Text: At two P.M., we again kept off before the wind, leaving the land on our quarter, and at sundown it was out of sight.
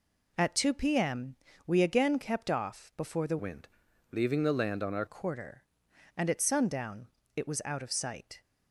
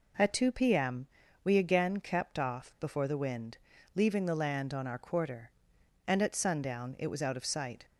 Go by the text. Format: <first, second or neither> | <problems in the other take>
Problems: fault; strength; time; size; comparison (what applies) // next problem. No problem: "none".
second | changes voice from "wind" to "our"; from 3.3 to 5.0 s; 1.7 s long // pauses between "sundown" and "it"; slight; at 7.0 s; 0.30 s long